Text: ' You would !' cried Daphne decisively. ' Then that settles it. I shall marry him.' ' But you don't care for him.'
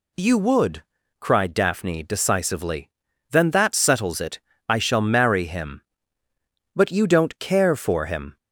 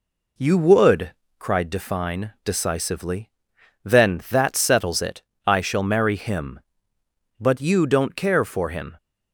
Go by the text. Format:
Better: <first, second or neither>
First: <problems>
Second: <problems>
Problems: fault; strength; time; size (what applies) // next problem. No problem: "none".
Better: first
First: none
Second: says "Define" for "Daphne"; at 1.7 s